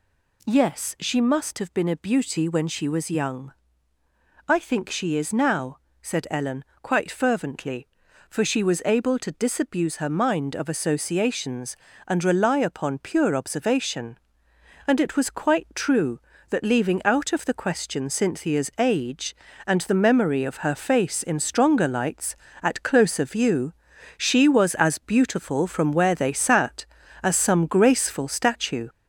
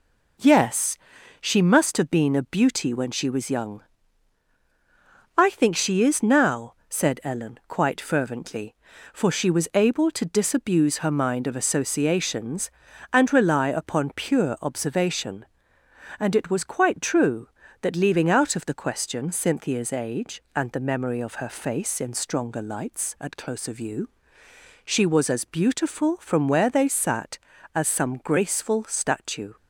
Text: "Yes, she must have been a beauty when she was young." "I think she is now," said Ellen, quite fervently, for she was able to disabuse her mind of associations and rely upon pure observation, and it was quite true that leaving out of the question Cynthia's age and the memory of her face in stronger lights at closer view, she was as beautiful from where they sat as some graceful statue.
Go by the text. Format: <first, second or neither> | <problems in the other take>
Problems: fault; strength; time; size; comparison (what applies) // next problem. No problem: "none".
second | gets louder; noticeable; throughout; 4 dB